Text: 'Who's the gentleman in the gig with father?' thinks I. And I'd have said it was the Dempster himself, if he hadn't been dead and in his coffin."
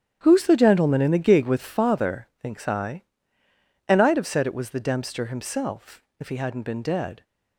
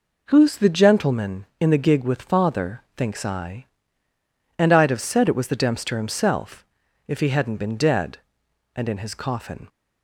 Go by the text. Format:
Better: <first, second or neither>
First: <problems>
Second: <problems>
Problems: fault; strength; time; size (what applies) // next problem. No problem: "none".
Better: second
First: starts louder than the rest; strong; until 1.2 s; 9.5 dB // stops before "and in his coffin"; at 7.2 s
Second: none